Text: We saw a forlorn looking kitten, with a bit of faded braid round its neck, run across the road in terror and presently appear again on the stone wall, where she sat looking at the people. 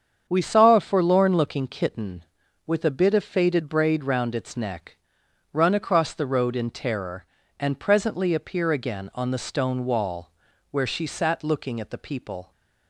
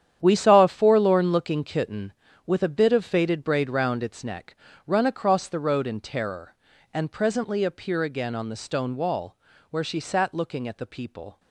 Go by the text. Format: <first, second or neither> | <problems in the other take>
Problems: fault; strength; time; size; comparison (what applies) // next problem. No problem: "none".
first | gets quieter; strong; throughout; 12.5 dB // starts louder than the rest; strong; until 1.2 s; 9.5 dB; strong in the first